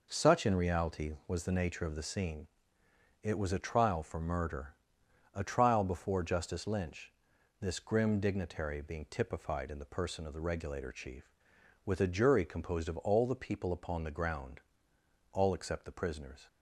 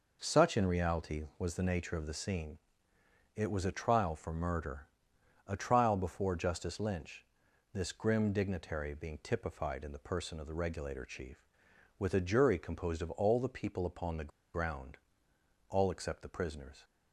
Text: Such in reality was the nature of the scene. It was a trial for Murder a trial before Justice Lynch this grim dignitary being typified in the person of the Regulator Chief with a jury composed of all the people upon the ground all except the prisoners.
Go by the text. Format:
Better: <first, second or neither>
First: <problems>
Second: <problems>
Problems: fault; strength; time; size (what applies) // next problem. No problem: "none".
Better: first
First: pauses between "Murder" and "a"; noticeable; at 4.7 s; 0.60 s long // pauses between "Lynch" and "this"; noticeable; at 7.1 s; 0.48 s long // pauses between "ground" and "all"; noticeable; at 14.6 s; 0.72 s long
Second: pauses between "Murder" and "a"; noticeable; at 4.8 s; 0.60 s long // pauses between "Lynch" and "this"; noticeable; at 7.2 s; 0.48 s long // pauses between "the" and "ground"; slight; at 14.3 s; 0.23 s long // pauses between "ground" and "all"; noticeable; at 14.9 s; 0.72 s long